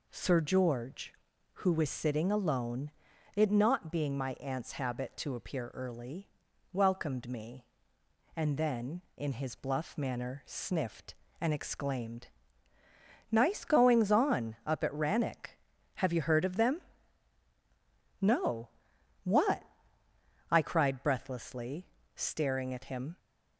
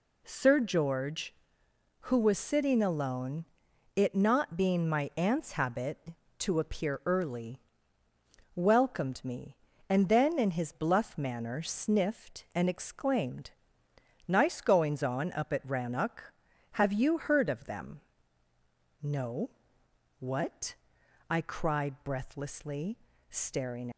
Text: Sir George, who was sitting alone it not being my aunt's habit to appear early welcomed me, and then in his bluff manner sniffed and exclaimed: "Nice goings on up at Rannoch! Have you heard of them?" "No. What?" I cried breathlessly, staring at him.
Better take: first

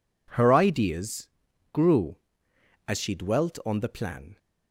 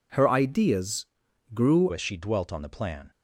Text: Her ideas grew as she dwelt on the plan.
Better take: first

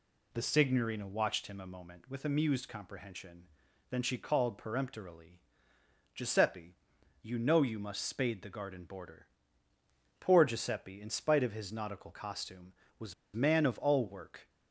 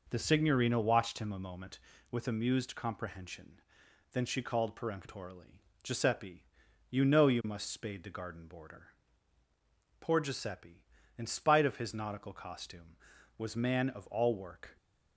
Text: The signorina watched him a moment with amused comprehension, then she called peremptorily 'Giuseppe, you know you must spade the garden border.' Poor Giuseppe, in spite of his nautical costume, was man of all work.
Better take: second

